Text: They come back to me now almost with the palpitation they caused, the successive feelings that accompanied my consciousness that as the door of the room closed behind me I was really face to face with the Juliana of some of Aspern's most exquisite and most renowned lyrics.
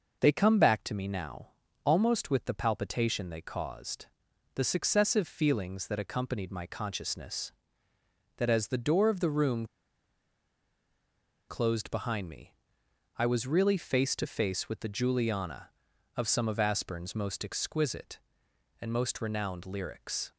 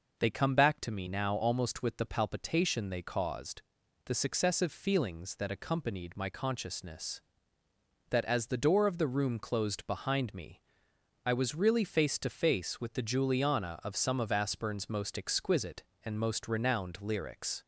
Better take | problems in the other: second | pauses between "now" and "almost"; at 1.4 s; 0.38 s long // pauses between "room" and "closed"; strong; at 9.6 s; 1.8 s long // pauses between "me" and "I"; noticeable; at 12.5 s; 0.64 s long; noticeable in the second

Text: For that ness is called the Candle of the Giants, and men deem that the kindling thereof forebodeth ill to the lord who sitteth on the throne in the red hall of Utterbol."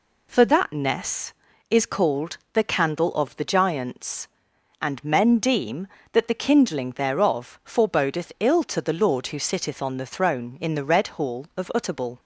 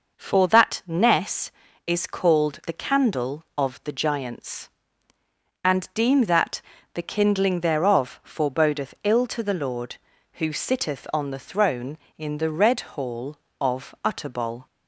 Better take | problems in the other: first | skips "men"; at 5.9 s // pauses between "that" and "the"; slight; at 6.6 s; 0.32 s long

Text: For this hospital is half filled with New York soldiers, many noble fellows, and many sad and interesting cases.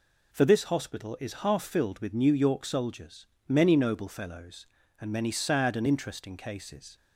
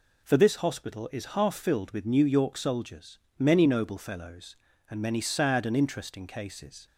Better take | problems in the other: neither | none

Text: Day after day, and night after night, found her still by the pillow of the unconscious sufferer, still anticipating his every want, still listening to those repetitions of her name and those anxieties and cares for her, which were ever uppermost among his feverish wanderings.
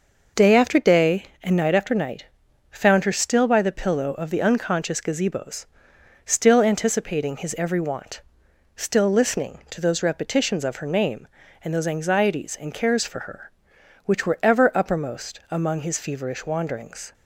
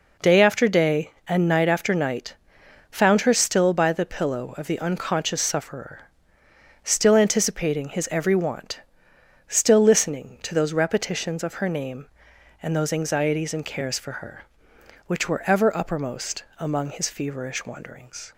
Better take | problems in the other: second | says "gazebos" for "sufferer"; at 4.9 s

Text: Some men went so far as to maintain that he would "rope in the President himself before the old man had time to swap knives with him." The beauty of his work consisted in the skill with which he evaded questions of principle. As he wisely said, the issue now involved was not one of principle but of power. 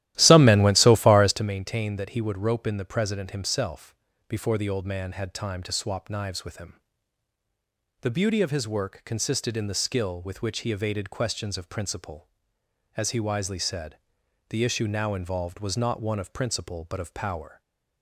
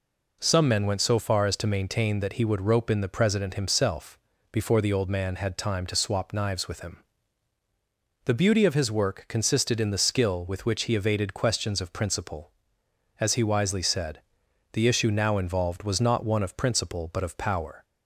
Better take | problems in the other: second | starts louder than the rest; strong; until 1.5 s; 14.5 dB // pauses between "himself" and "before"; slight; at 3.9 s; 0.34 s long; slight in the second // stays silent after the last word; slight; from 17.5 s on; 0.5 s long

